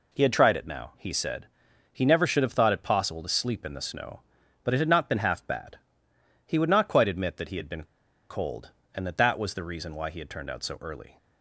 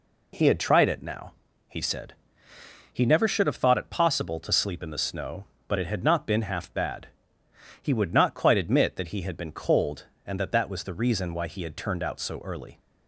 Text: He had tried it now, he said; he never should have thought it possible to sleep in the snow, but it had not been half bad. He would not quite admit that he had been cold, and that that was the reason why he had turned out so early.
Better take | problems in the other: second | pauses between "been" and "cold"; at 7.8 s; 0.45 s long

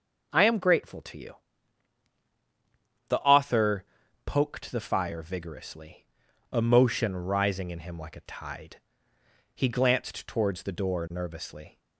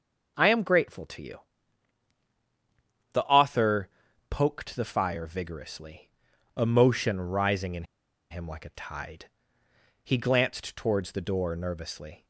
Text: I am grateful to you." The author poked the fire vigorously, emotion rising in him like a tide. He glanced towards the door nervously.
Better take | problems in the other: first | pauses between "author" and "poked"; at 3.8 s; 0.42 s long; also in the first // pauses between "in" and "him"; noticeable; at 7.8 s; 0.46 s long

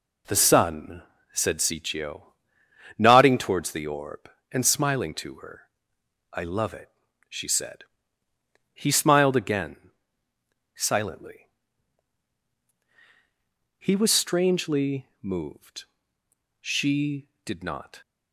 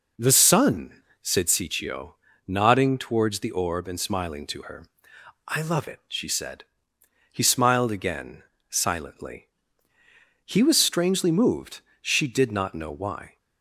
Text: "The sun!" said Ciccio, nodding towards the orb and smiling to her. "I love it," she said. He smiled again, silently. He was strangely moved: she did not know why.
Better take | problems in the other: second | stops before "know why"; at 18.0 s

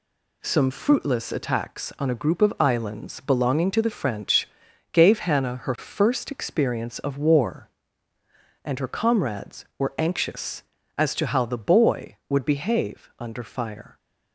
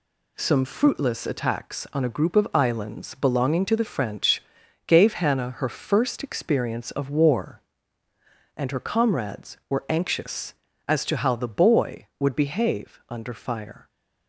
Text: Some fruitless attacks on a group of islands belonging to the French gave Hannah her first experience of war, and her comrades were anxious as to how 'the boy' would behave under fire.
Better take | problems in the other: neither | pauses between "French" and "gave"; noticeable; the same in both

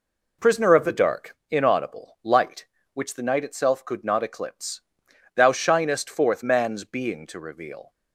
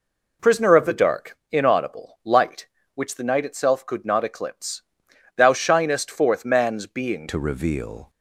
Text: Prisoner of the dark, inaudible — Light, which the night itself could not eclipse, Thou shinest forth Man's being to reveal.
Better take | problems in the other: first | changes voice at "to"; from 7.2 s on; 0.8 s long

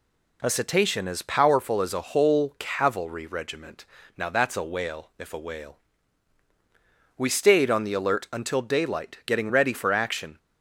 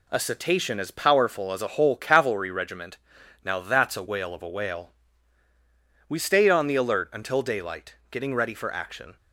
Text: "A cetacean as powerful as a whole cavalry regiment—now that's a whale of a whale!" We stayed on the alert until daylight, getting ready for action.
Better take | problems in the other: second | says "if" for "of"; at 5.1 s

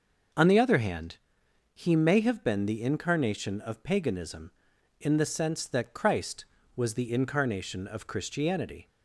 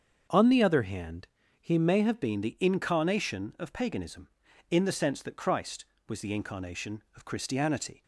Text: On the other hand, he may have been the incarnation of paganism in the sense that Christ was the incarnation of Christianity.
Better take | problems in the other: first | starts louder than the rest; until 1.6 s; 7 dB // changes voice at "been"; from 2.2 s on; 5.8 s long

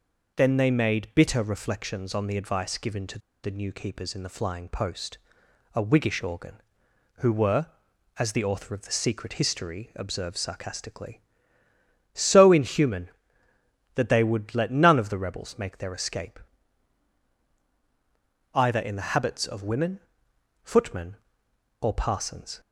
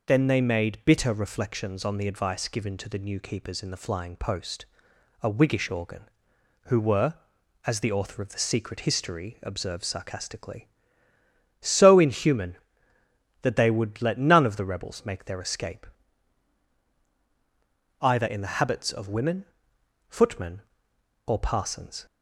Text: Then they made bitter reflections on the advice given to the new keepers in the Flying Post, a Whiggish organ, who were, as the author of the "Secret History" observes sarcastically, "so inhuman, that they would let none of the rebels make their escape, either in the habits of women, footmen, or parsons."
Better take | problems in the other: second | pauses between "to" and "the"; slight; at 3.1 s; 0.24 s long

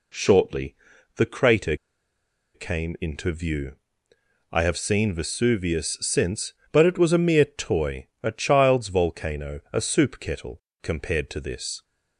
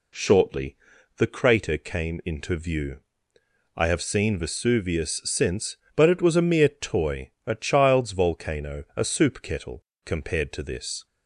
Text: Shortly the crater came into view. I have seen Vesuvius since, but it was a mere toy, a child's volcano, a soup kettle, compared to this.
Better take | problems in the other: second | pauses between "Shortly" and "the"; at 0.7 s; 0.42 s long; also in the second // pauses between "crater" and "came"; noticeable; at 1.7 s; 0.79 s long

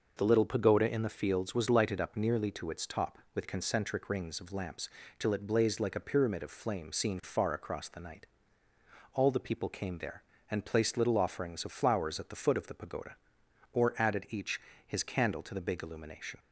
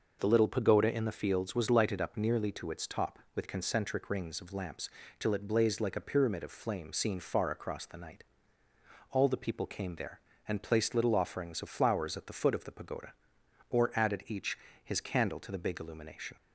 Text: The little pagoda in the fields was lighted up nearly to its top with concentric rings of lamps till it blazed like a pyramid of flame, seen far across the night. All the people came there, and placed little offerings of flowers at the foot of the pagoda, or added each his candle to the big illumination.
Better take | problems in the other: neither | pauses between "lamps" and "till"; slight; the same in both // pauses between "each" and "his"; slight; the same in both

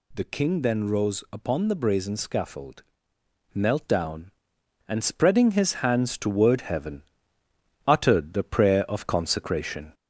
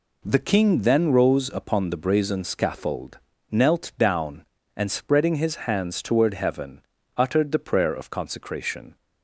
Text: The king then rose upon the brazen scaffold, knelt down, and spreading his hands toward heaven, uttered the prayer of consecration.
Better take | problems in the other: second | gets louder; slight; throughout; 2.5 dB

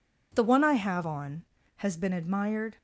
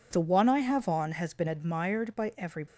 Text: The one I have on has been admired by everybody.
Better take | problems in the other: second | stops before "by everybody"; at 2.7 s

